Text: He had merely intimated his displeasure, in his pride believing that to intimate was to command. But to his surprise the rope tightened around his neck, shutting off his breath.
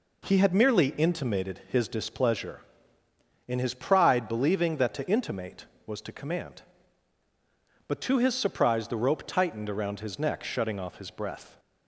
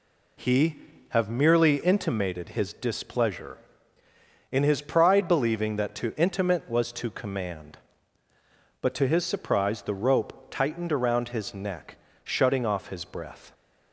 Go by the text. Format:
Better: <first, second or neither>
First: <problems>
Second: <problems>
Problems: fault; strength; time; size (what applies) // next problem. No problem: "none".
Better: first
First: none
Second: says "have" for "had"; at 1.0 s